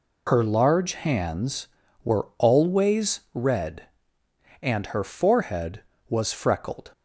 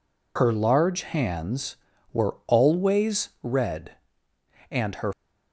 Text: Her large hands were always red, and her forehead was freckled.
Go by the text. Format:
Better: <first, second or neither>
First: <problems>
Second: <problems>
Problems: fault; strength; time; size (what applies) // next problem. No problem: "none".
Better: first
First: none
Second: stops before "forehead was freckled"; at 5.1 s